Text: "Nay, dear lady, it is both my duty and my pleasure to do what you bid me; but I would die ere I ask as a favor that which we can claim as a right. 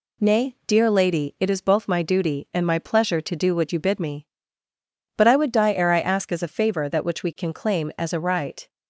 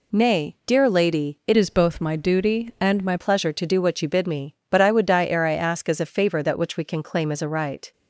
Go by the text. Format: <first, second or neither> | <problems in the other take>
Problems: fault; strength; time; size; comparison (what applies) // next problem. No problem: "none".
first | changes voice from "is" to "my"; from 1.5 to 3.1 s; 1.6 s long